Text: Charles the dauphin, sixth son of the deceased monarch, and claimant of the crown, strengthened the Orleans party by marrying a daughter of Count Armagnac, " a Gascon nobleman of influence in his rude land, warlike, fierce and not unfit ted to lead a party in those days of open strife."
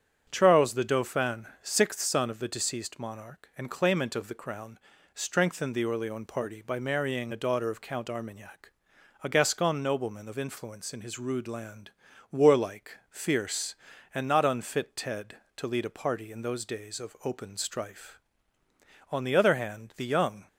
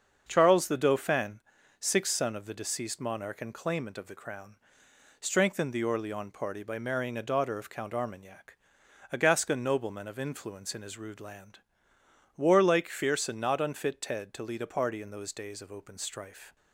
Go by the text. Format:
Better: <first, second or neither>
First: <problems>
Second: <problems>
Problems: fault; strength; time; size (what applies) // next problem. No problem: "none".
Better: second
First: starts louder than the rest; strong; until 1.2 s; 8.5 dB // goes on to say "On the other hand the young"; from 19.1 s on; 1.3 s long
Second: starts louder than the rest; until 1.2 s; 7 dB